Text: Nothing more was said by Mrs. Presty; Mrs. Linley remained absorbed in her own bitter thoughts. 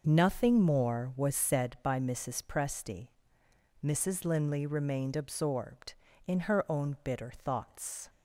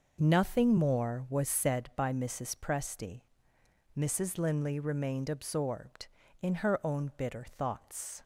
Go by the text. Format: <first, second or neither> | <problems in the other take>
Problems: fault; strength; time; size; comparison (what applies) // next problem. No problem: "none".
neither | none